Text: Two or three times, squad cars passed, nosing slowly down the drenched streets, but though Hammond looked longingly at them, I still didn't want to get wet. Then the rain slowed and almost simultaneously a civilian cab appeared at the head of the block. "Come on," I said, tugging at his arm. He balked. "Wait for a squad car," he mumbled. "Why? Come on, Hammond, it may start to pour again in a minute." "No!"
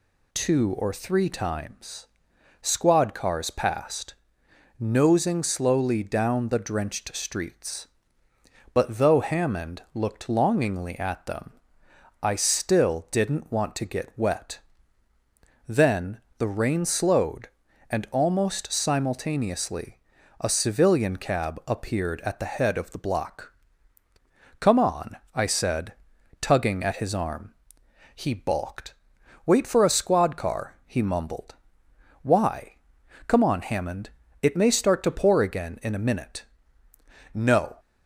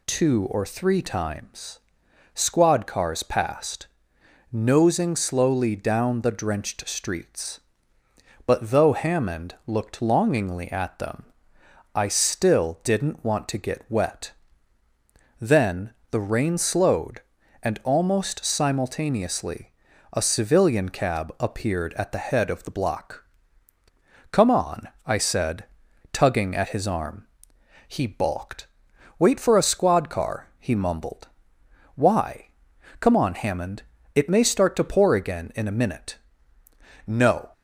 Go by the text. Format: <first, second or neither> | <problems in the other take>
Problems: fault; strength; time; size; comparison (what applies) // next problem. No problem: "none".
neither | pauses between "Then" and "the"; slight; the same in both // pauses between "simultaneously" and "a"; the same in both